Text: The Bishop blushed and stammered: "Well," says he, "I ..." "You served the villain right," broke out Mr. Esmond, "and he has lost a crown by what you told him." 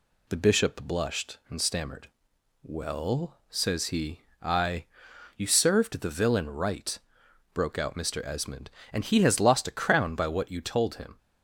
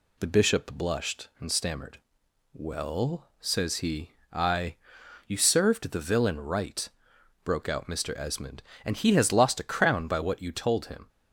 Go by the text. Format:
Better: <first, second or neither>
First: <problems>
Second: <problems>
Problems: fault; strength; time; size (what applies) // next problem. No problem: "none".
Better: neither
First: none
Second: none